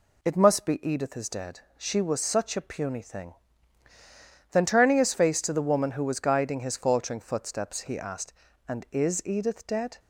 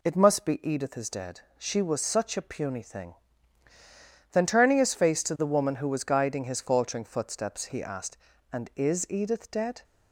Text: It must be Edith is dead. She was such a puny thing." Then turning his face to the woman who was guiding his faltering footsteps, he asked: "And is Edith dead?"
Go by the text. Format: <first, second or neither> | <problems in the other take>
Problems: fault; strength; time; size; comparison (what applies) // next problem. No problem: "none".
neither | none